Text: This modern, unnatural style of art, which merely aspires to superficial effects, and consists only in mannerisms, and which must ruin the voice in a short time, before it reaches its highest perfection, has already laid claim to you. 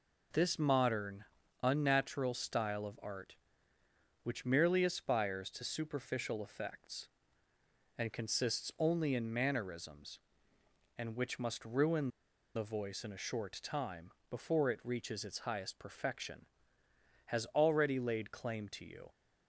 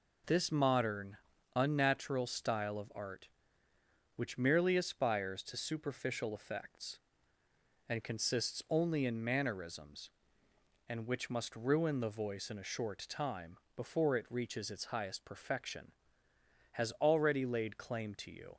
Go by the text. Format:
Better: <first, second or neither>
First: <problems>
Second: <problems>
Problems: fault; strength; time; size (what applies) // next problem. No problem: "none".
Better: second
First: pauses between "ruin" and "the"; noticeable; at 12.0 s; 0.47 s long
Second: none